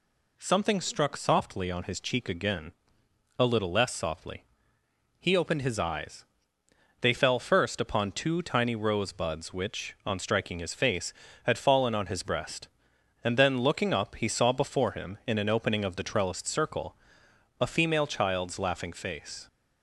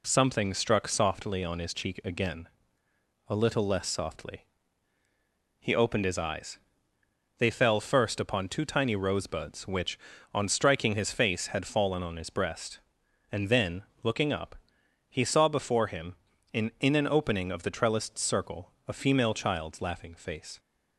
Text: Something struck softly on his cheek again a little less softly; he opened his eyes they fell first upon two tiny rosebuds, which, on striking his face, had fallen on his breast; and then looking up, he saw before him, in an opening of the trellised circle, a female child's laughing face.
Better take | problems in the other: first | pauses between "again" and "a"; noticeable; at 2.4 s; 0.80 s long; noticeable in the first // pauses between "eyes" and "they"; noticeable; at 6.5 s; 0.80 s long; noticeable in the first // pauses between "then" and "looking"; slight; at 13.8 s; 0.22 s long // says "in" twice; at 16.7 s

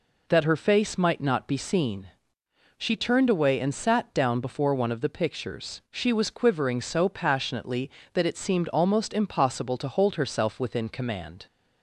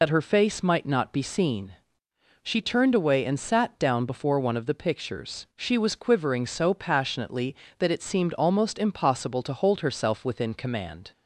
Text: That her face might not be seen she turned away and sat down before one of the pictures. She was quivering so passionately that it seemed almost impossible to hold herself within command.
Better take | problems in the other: first | loses the start of "That"; at 0.0 s; 80 ms // pauses between "seen" and "she"; noticeable; at 1.7 s; 0.70 s long; noticeable in the first

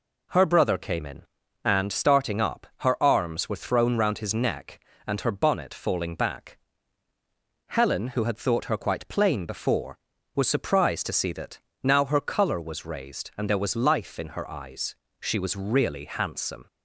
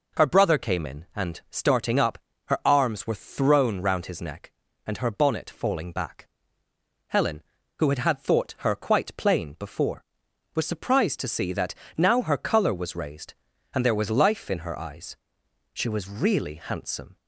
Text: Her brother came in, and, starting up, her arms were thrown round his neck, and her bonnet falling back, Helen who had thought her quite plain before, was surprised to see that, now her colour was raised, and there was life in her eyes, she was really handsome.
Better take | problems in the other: first | says "had" twice; at 7.9 s

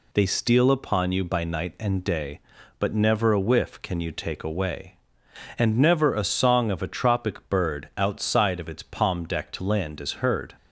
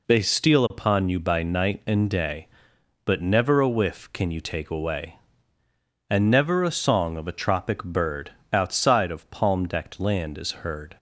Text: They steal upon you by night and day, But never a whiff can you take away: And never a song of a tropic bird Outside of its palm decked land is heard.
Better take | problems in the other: first | pauses between "bird" and "Outside"; slight; at 8.3 s; 0.22 s long // skips "its"; at 9.3 s

